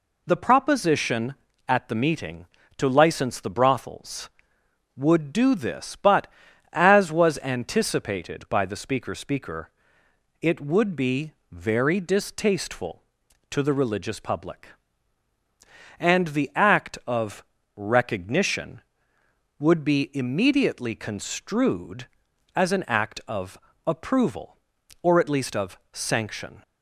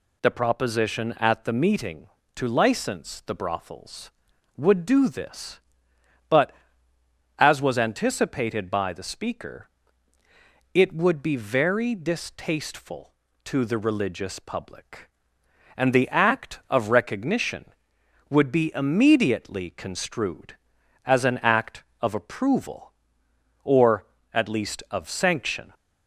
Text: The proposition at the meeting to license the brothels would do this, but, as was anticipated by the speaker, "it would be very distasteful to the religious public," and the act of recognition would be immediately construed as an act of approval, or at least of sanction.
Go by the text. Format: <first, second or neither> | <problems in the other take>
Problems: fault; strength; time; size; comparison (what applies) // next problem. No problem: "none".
second | says "speaker" twice; at 9.1 s // pauses between "be" and "very"; slight; at 11.3 s; 0.18 s long // pauses between "of" and "recognition"; slight; at 17.4 s; 0.32 s long // pauses between "of" and "approval"; slight; at 23.5 s; 0.28 s long